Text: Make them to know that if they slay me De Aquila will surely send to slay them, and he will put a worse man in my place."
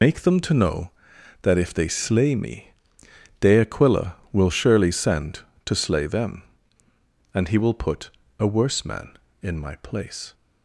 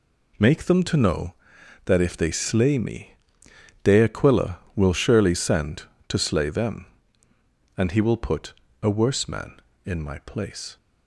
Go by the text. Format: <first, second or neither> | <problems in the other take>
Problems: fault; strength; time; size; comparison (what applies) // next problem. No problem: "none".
second | loses the start of "Make"; at 0.0 s; 95 ms // pauses between "me" and "De"; noticeable; at 2.7 s; 0.68 s long; noticeable in the second // pauses between "put" and "a"; slight; at 8.0 s; 0.28 s long; slight in the second